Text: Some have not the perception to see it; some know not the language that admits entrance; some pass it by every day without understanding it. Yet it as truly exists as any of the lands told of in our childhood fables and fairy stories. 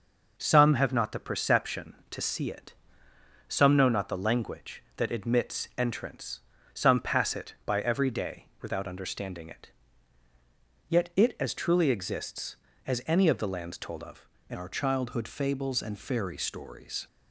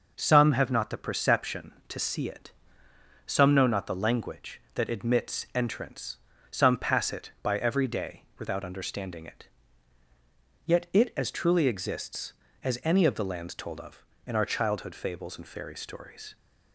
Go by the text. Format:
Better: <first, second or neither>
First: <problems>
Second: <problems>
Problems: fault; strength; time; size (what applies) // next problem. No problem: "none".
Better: second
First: changes voice at "our"; from 14.5 s on; 2.5 s long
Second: none